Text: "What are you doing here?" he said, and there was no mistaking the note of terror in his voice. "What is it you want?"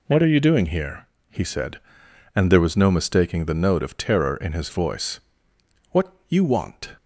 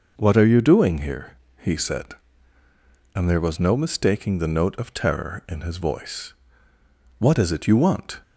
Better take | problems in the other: second | skips "is it"; at 6.2 s

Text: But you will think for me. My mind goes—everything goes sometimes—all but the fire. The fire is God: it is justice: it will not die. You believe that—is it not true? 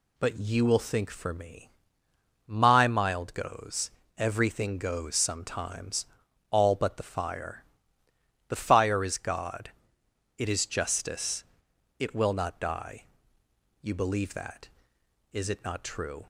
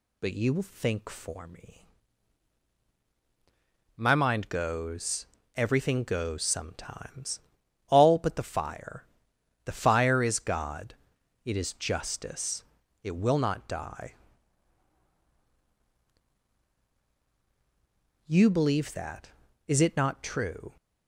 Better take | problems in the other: second | says "mild" for "mind"; at 2.8 s

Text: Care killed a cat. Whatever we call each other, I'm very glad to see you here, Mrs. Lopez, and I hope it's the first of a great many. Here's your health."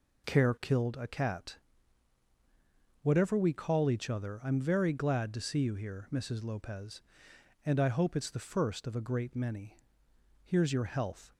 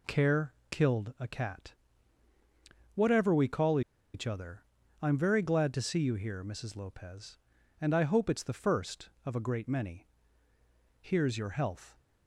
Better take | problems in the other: first | pauses between "Care" and "killed"; slight; at 0.5 s; 0.18 s long // pauses between "call" and "each"; slight; at 3.8 s; 0.33 s long

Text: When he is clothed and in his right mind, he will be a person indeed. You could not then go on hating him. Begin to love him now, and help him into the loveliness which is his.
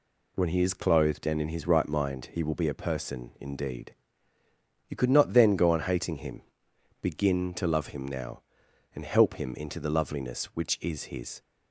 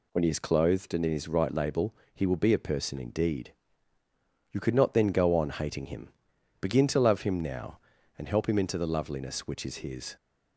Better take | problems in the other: first | says "label" for "mind"; at 1.5 s

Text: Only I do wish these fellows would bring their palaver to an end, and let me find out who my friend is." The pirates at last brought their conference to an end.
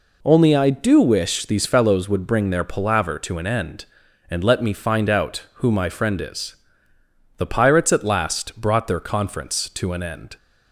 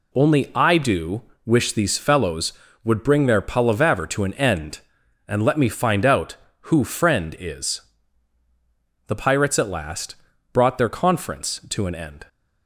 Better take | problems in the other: first | pauses between "do" and "wish"; slight; at 1.2 s; 0.24 s long // skips "my"; at 6.8 s // pauses between "last" and "brought"; slight; at 10.1 s; 0.36 s long

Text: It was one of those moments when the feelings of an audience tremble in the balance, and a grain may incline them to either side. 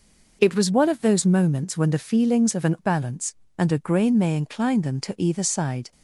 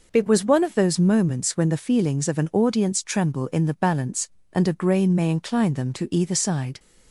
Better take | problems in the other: second | skips "audience tremble in the"; at 2.7 s

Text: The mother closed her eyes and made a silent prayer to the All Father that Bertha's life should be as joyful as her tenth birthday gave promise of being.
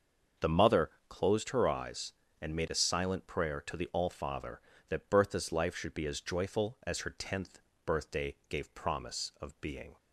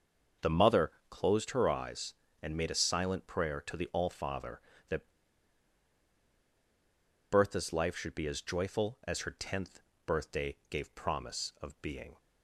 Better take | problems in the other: first | starts louder than the rest; until 1.5 s; 6.5 dB; also in the first // pauses between "mother" and "closed"; slight; at 0.9 s; 0.18 s long; slight in the first // pauses between "that" and "Bertha's"; strong; at 5.1 s; 2.2 s long // pauses between "tenth" and "birthday"; slight; at 9.8 s; 0.24 s long; slight in the first

